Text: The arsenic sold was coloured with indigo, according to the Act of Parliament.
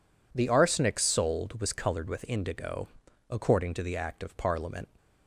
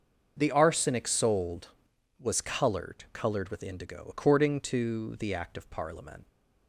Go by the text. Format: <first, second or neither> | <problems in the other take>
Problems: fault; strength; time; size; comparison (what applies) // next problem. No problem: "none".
first | starts louder than the rest; until 1.3 s; 6.5 dB // says "coloured" twice; at 3.1 s